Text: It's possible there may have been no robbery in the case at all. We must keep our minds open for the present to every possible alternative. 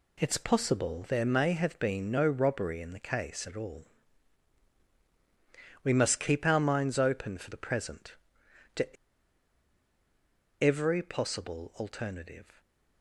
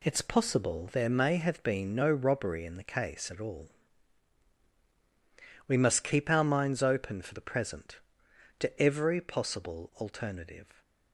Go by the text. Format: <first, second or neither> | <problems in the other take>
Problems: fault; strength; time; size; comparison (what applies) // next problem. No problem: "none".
second | pauses between "to" and "every"; strong; at 8.9 s; 1.6 s long